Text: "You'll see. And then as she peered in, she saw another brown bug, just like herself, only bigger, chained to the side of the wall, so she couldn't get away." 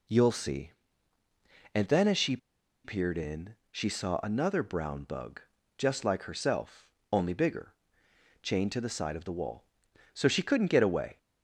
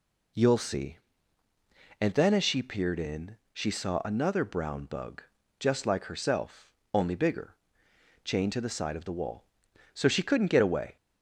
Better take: second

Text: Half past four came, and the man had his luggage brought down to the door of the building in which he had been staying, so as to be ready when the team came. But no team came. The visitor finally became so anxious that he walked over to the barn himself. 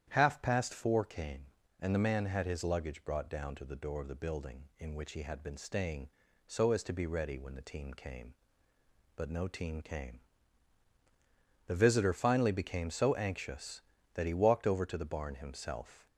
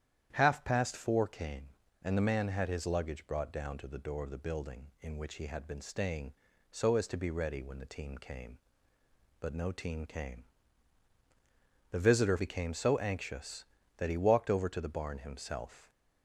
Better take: first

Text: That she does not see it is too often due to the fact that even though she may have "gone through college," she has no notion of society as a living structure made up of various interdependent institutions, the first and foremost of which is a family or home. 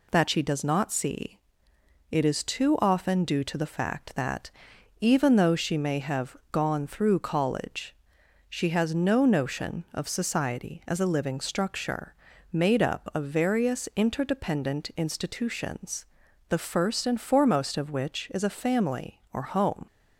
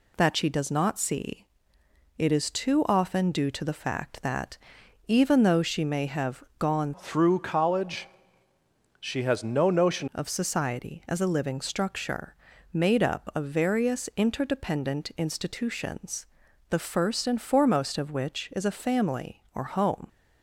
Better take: first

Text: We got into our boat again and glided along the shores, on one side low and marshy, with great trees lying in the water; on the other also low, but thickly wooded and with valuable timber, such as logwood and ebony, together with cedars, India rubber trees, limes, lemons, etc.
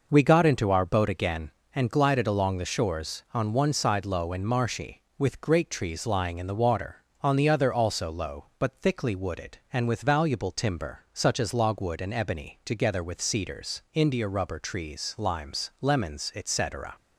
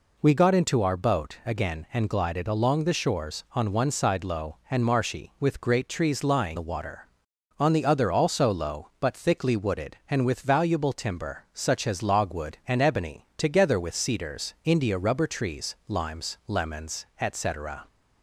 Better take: first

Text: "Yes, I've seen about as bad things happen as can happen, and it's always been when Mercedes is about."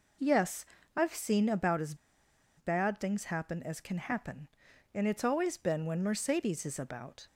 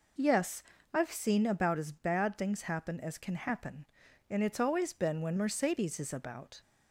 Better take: second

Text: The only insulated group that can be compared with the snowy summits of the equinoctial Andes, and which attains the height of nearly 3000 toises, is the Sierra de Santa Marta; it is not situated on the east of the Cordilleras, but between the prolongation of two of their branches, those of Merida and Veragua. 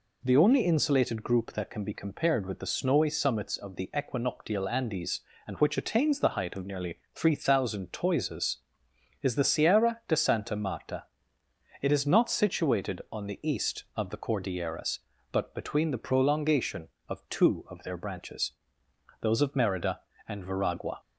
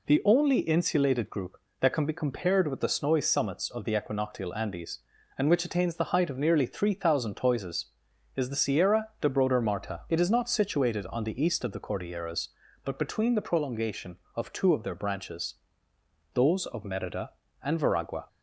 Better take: first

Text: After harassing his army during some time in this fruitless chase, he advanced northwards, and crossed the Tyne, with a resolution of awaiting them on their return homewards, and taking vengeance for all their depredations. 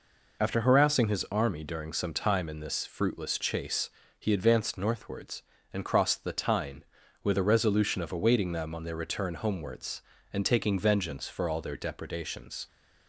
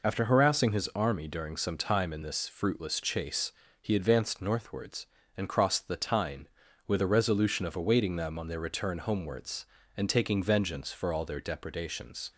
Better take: neither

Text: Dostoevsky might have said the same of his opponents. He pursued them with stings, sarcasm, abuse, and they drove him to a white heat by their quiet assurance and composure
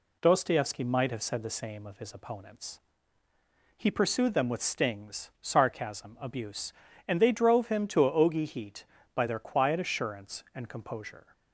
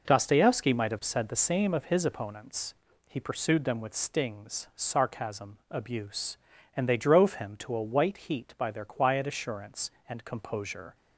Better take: second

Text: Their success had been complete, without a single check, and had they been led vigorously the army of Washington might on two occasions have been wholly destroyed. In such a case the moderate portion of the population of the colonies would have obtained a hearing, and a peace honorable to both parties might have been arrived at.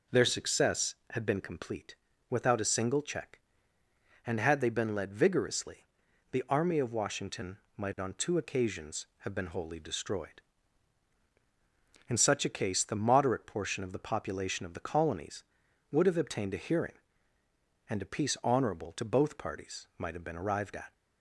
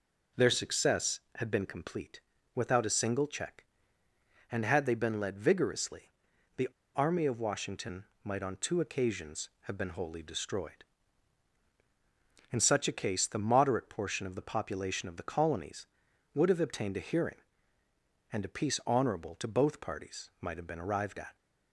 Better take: first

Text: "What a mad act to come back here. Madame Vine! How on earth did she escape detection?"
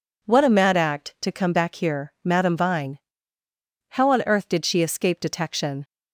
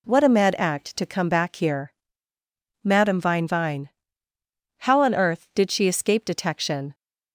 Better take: first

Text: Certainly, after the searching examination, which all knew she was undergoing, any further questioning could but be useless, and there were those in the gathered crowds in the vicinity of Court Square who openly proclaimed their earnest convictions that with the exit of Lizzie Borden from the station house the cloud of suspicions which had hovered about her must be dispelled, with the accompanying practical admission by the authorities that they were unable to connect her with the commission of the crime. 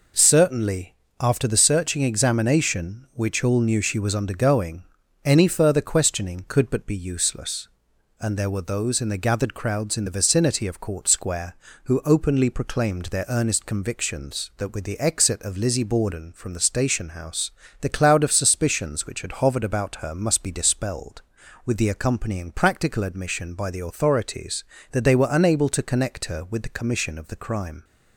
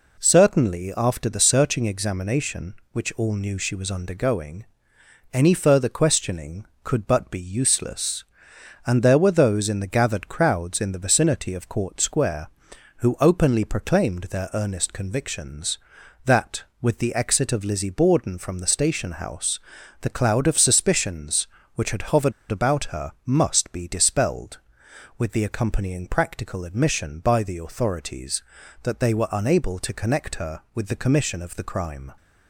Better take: first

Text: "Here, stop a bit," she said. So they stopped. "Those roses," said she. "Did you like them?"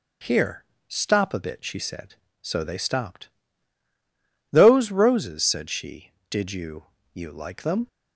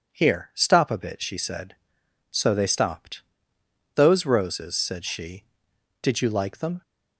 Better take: second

